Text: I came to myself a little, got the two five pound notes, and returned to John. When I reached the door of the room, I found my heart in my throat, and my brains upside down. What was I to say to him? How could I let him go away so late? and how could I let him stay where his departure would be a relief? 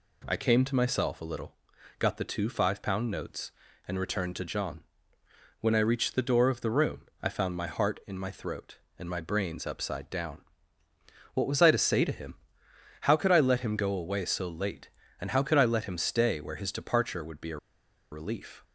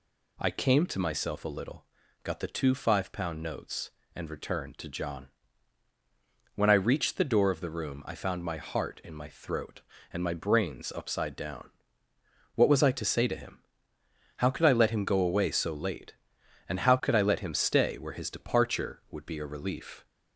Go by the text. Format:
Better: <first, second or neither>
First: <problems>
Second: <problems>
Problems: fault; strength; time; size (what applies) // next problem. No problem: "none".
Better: second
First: pauses between "a" and "relief"; noticeable; at 17.5 s; 0.55 s long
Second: none